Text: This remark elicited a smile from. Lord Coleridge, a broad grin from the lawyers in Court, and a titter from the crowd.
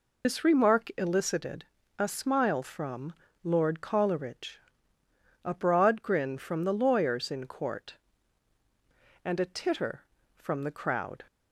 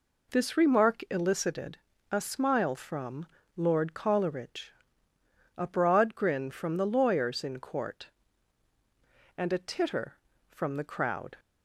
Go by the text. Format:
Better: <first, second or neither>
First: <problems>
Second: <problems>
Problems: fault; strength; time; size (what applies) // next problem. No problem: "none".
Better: second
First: loses the start of "This"; at 0.2 s; 75 ms // pauses between "elicited" and "a"; slight; at 1.6 s; 0.34 s long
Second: pauses between "elicited" and "a"; slight; at 1.7 s; 0.34 s long